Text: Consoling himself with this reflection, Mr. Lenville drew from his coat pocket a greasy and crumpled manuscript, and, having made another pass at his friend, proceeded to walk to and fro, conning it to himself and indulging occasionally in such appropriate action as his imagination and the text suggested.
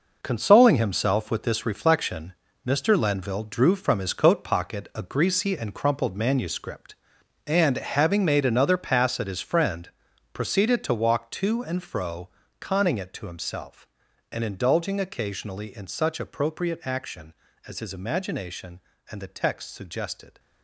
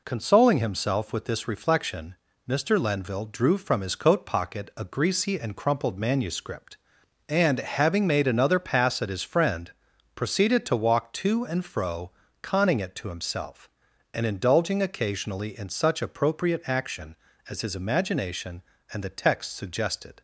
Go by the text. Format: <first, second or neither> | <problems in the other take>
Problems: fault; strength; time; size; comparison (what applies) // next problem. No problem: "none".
second | gets quieter; strong; throughout; 9.5 dB